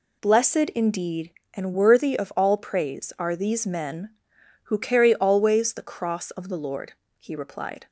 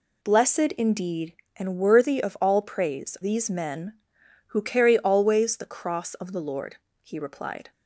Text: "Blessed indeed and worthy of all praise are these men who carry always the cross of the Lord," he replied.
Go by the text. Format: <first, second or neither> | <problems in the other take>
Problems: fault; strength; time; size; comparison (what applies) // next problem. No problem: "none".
first | skips "are"; at 3.1 s